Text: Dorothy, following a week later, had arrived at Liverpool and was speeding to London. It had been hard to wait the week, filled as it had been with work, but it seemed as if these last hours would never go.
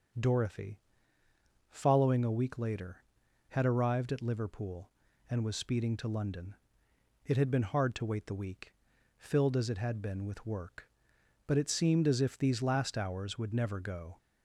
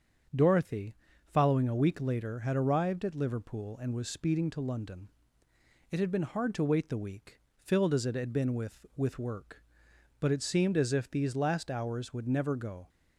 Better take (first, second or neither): first